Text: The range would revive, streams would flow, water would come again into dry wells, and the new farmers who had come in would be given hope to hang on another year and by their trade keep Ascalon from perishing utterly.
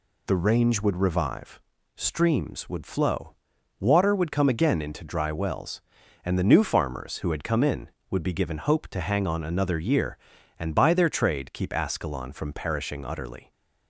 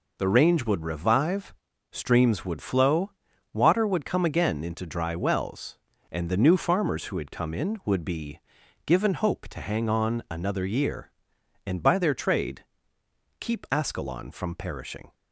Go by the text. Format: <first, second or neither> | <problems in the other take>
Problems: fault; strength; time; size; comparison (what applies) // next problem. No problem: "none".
first | pauses between "be" and "given"; noticeable; at 8.3 s; 0.46 s long // pauses between "trade" and "keep"; noticeable; at 12.6 s; 0.74 s long // stops before "utterly"; at 15.1 s